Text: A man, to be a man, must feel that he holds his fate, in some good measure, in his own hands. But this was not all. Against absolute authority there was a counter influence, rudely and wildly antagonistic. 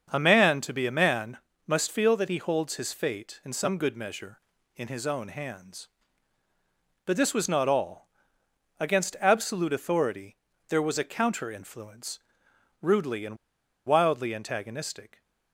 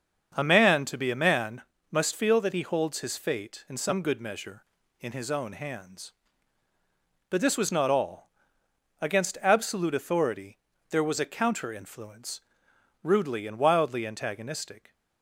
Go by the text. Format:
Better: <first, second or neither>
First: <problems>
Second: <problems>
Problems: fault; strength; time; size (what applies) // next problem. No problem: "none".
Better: second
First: starts louder than the rest; until 1.1 s; 6.5 dB // pauses between "authority" and "there"; slight; at 10.3 s; 0.32 s long // pauses between "and" and "wildly"; noticeable; at 13.3 s; 0.49 s long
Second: starts louder than the rest; until 1.3 s; 7 dB // pauses between "authority" and "there"; slight; at 10.5 s; 0.32 s long